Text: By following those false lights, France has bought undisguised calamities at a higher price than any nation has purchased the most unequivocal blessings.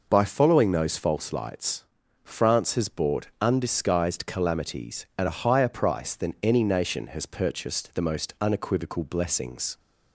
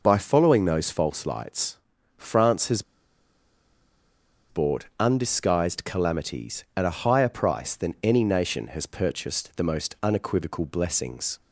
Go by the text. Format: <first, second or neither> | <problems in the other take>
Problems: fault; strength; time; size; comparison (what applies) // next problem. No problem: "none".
first | pauses between "has" and "bought"; strong; at 2.8 s; 1.6 s long